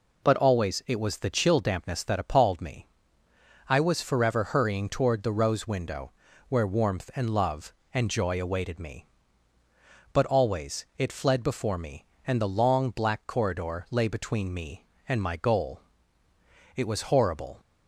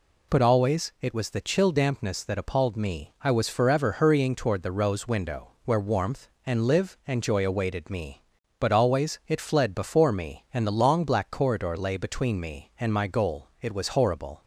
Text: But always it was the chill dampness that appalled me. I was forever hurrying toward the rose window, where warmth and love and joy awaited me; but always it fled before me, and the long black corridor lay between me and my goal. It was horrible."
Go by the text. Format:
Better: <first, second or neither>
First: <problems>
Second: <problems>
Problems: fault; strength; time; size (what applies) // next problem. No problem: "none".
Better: first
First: none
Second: says "live" for "love"; at 6.6 s